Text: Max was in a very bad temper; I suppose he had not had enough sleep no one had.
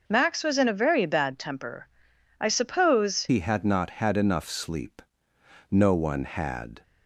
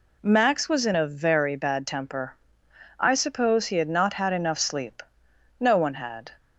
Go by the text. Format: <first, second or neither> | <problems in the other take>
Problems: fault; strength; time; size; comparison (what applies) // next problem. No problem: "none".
second | changes voice at "he"; from 3.2 s on; 3.6 s long // pauses between "sleep" and "no"; noticeable; at 5.0 s; 0.70 s long; noticeable in the second